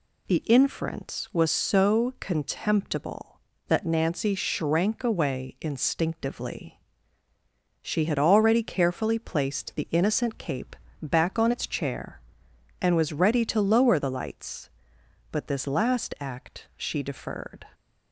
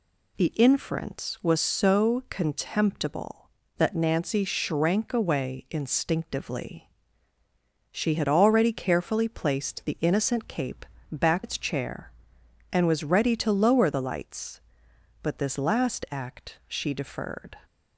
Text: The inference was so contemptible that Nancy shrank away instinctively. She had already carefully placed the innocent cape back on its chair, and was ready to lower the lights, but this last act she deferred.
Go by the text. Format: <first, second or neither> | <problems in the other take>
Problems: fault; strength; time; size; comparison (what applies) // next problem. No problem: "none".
first | pauses between "cape" and "back"; slight; at 10.8 s; 0.24 s long; slight in the first // skips "on"; at 11.4 s